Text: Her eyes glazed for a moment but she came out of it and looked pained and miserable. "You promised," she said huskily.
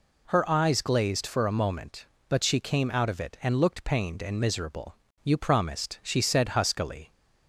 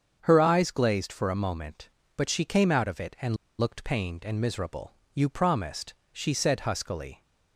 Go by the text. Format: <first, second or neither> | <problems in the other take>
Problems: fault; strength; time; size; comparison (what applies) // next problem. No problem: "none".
first | starts louder than the rest; strong; until 1.2 s; 7 dB // pauses between "and" and "looked"; slight; at 3.3 s; 0.23 s long